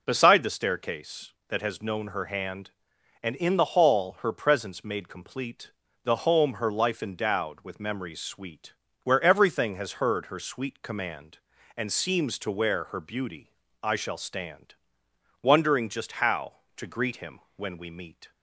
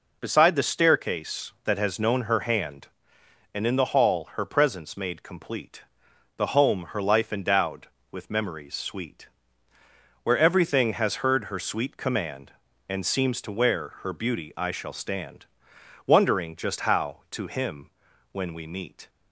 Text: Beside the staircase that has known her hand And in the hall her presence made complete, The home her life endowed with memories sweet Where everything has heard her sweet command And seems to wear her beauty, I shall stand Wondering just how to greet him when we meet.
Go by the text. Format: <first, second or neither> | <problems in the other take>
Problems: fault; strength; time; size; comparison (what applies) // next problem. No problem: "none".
first | pauses between "sweet" and "Where"; noticeable; at 9.2 s; 0.96 s long; slight in the first // pauses between "stand" and "Wondering"; noticeable; at 15.4 s; 0.60 s long; noticeable in the first // skips "greet"; at 17.4 s // pauses between "him" and "when"; at 17.8 s; 0.42 s long; slight in the first